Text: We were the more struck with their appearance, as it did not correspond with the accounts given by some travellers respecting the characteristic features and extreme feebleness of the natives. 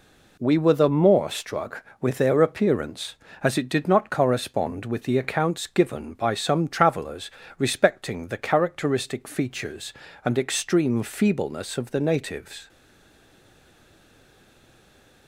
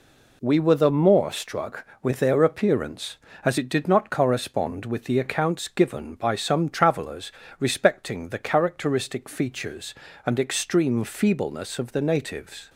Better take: second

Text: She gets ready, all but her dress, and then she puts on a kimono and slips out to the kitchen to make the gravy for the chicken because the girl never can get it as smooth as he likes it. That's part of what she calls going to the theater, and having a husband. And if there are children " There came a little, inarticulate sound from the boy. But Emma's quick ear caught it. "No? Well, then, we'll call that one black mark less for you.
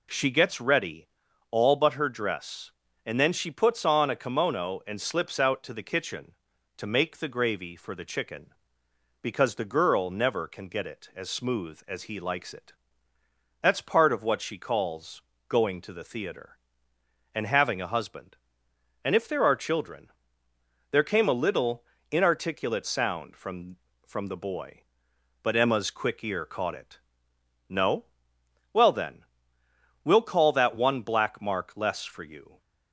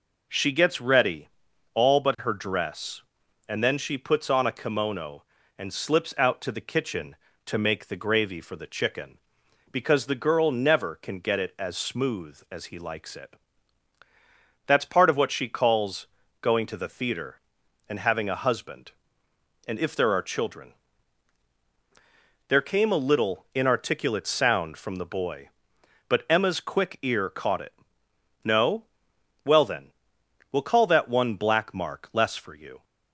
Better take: second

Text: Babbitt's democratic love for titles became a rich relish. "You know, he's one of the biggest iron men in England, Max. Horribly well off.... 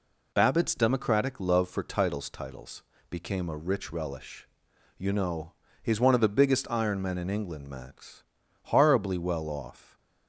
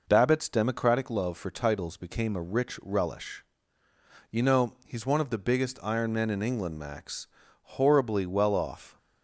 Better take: second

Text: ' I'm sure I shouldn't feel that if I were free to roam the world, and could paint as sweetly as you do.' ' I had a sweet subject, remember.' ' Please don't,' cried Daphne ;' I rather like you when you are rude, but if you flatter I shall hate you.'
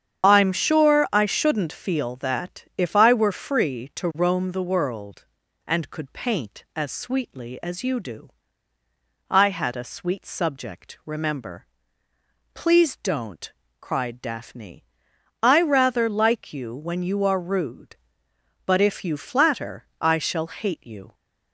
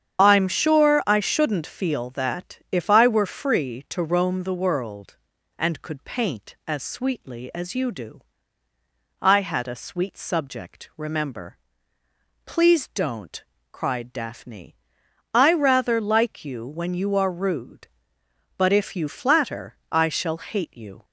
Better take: neither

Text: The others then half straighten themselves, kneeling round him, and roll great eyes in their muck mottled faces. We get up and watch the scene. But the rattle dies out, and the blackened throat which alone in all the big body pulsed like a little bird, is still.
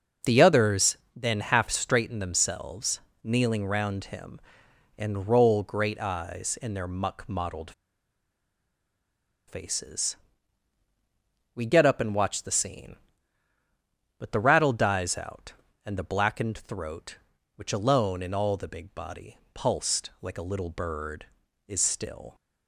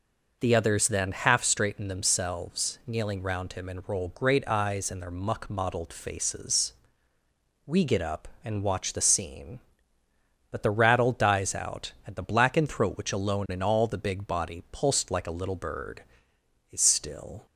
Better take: second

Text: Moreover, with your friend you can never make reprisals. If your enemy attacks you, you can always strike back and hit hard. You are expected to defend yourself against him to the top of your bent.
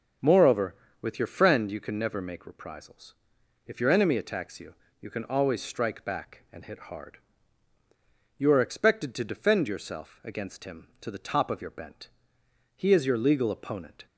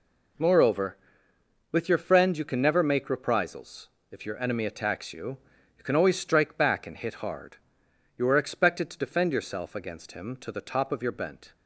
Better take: second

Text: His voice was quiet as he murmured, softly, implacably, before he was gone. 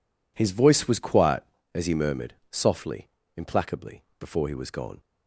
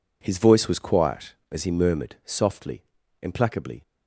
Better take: first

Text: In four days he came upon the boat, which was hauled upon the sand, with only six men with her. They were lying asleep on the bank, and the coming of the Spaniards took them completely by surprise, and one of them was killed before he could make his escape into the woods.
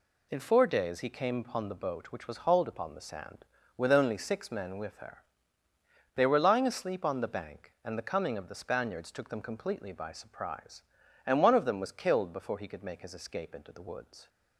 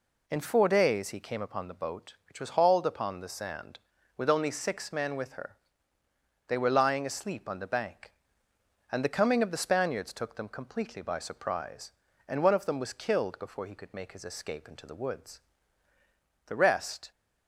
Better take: first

